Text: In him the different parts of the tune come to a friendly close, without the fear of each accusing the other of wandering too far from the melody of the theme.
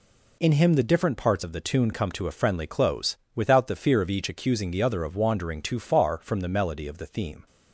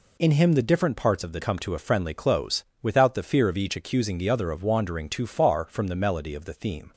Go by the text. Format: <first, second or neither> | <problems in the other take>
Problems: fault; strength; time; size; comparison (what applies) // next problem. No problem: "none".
first | skips "tune"; at 1.4 s